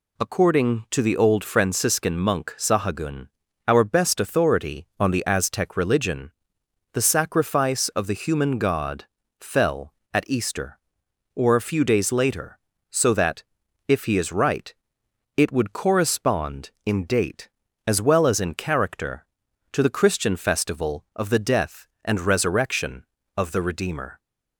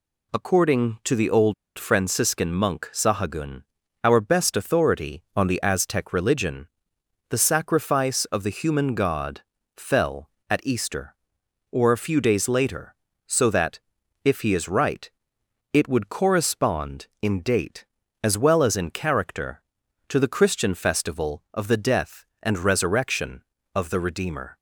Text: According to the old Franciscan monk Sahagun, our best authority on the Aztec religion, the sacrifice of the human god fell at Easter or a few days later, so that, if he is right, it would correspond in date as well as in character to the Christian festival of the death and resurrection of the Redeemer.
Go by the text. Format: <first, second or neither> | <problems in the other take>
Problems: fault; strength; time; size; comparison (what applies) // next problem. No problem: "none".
first | pauses between "old" and "Franciscan"; slight; at 1.5 s; 0.24 s long // pauses between "god" and "fell"; slight; at 9.4 s; 0.34 s long; slight in the first